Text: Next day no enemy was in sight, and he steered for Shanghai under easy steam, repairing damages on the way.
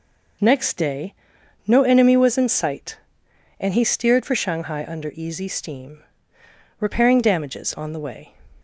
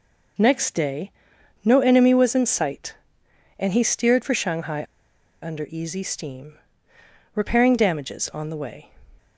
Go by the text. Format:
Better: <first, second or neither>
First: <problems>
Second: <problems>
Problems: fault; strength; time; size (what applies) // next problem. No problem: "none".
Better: first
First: pauses between "day" and "no"; noticeable; at 1.1 s; 0.52 s long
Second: pauses between "day" and "no"; noticeable; at 1.1 s; 0.52 s long // pauses between "Shanghai" and "under"; noticeable; at 4.8 s; 0.58 s long